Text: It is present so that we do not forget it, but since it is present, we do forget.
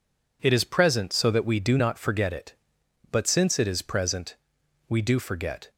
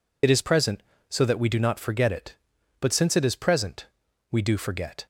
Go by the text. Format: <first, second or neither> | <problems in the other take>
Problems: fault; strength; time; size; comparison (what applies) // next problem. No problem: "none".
first | loses the start of "It"; at 0.2 s; 45 ms